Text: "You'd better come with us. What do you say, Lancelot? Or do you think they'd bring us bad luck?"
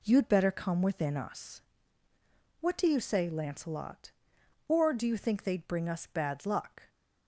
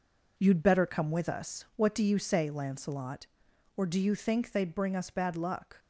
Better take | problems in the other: second | says "within" for "with"; at 0.8 s

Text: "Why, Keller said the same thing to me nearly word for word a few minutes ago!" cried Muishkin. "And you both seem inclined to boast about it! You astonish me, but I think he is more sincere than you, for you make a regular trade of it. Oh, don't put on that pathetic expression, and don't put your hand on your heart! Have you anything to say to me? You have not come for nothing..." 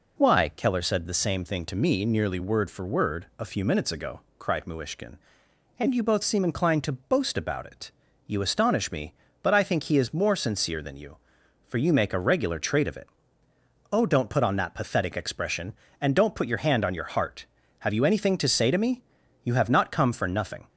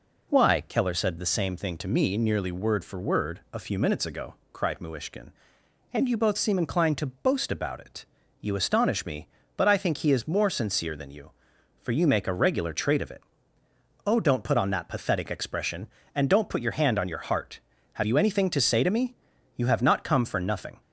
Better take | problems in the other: neither | none

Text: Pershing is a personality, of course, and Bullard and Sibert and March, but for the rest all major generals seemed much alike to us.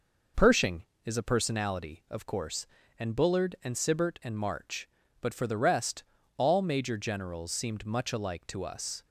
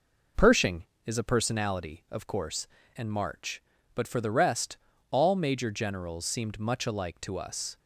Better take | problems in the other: first | skips "and Bullard and Sibert"; at 2.8 s // pauses between "rest" and "all"; slight; at 4.7 s; 0.34 s long; slight in the first

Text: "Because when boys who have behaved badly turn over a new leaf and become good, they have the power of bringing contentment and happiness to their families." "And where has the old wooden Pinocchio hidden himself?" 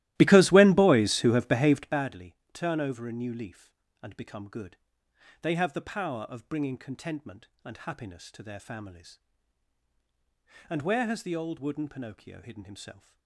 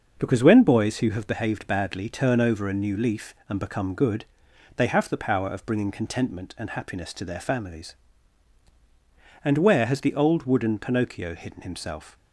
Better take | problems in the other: second | starts louder than the rest; strong; until 2.1 s; 15.5 dB // pauses between "badly" and "turn"; slight; at 2.3 s; 0.18 s long

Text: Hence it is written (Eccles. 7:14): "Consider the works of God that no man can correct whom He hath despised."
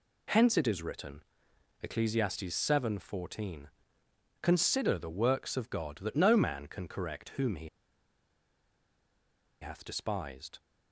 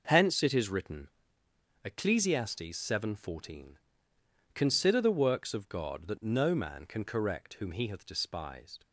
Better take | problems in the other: second | pauses between "He" and "hath"; strong; at 7.6 s; 1.9 s long

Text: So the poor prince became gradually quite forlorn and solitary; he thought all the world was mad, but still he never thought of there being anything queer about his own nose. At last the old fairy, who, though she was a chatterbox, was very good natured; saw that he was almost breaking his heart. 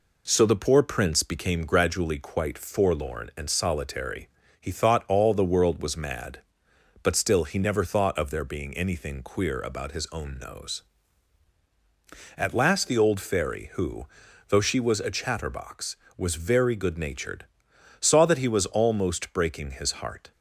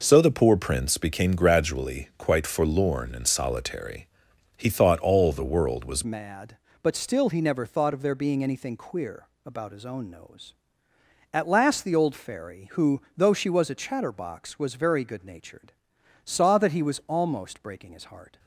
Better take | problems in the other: first | changes voice at "mad"; from 6.0 s on; 12.3 s long // pauses between "queer" and "about"; slight; at 9.2 s; 0.18 s long

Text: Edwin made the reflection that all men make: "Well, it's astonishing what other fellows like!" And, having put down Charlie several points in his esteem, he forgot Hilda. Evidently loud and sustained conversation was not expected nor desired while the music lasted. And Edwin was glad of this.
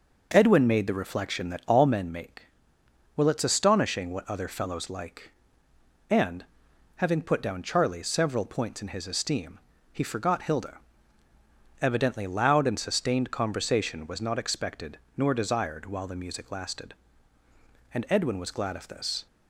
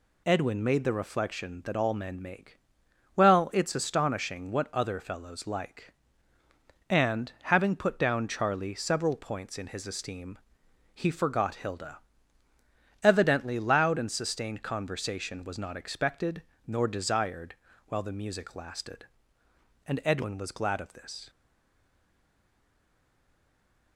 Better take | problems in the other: first | pauses between "expected" and "nor"; slight; at 16.4 s; 0.24 s long; slight in the first // pauses between "desired" and "while"; slight; at 17.5 s; 0.32 s long // stays silent after the last word; strong; from 21.2 s on; 2.7 s long

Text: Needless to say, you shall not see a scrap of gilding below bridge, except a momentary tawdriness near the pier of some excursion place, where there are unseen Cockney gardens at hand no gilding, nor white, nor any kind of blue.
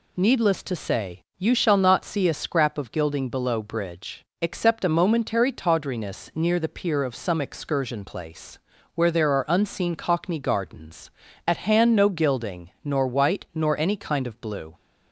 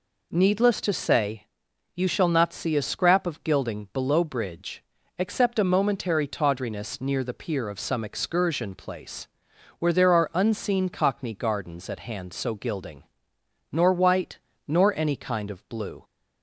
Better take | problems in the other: first | says "so" for "no"; at 12.3 s

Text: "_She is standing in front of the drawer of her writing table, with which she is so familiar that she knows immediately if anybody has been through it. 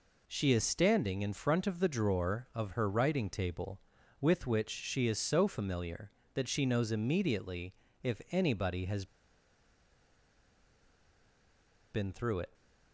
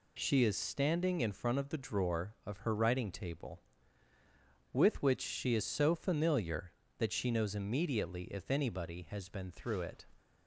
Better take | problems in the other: second | pauses between "immediately" and "if"; slight; at 7.7 s; 0.26 s long // pauses between "has" and "been"; strong; at 9.0 s; 2.8 s long

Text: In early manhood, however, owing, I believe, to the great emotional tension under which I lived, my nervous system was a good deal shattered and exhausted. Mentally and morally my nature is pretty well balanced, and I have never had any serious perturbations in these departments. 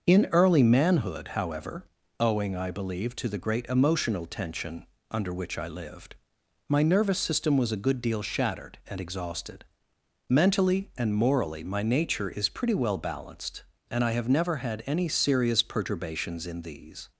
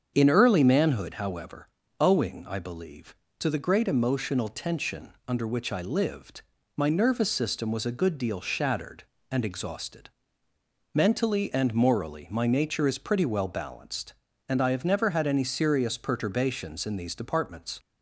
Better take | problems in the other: second | starts louder than the rest; until 1.1 s; 6.5 dB; strong in the second // pauses between "tension" and "under"; slight; at 4.8 s; 0.24 s long // stops before "departments"; at 17.1 s

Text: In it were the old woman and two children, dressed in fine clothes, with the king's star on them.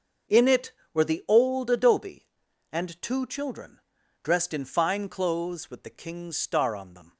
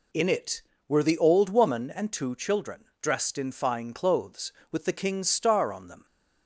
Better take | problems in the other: second | starts louder than the rest; until 1.5 s; 6.5 dB // says "adobe" for "woman"; at 1.6 s

